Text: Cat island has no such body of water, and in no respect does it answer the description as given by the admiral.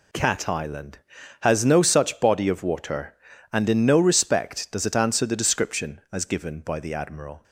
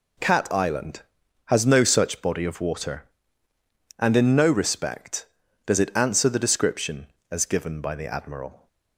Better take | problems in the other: neither | none

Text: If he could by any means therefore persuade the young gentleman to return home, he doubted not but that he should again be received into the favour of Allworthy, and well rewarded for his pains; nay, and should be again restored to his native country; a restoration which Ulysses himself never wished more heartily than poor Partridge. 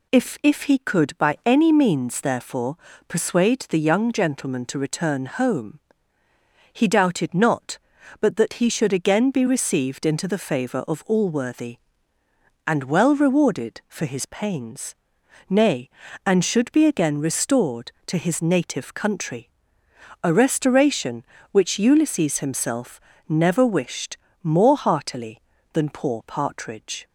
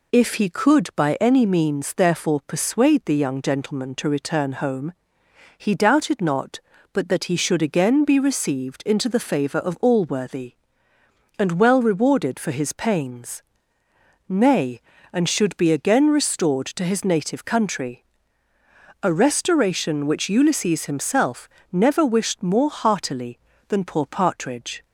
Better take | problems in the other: second | says "If" twice; at 0.4 s // pauses between "therefore" and "persuade"; slight; at 2.7 s; 0.32 s long // pauses between "himself" and "never"; slight; at 22.9 s; 0.28 s long; slight in the second // pauses between "wished" and "more"; slight; at 24.1 s; 0.26 s long

